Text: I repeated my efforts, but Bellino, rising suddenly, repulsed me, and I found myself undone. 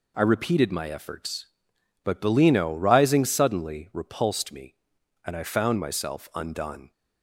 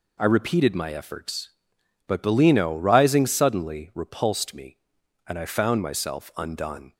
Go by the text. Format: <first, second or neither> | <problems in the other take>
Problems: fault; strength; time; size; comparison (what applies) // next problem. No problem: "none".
neither | none